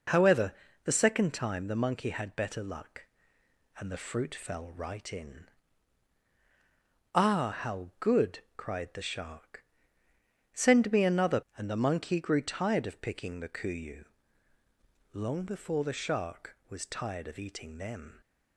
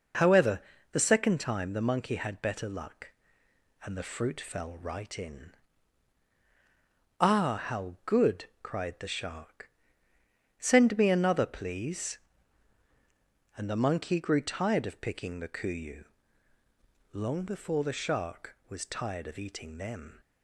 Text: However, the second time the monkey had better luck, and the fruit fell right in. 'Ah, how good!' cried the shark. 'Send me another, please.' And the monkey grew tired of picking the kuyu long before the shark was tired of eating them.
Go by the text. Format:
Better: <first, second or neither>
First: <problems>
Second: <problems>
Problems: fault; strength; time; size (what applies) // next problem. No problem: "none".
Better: second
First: skips "please"; at 11.4 s // pauses between "kuyu" and "long"; at 14.0 s; 1.0 s long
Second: pauses between "kuyu" and "long"; at 16.0 s; 1.0 s long